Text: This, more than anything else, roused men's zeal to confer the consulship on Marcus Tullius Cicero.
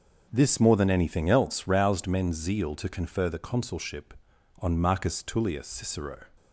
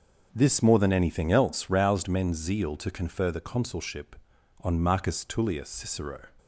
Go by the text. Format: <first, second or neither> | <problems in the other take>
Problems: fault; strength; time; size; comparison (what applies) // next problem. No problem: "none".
neither | starts louder than the rest; the same in both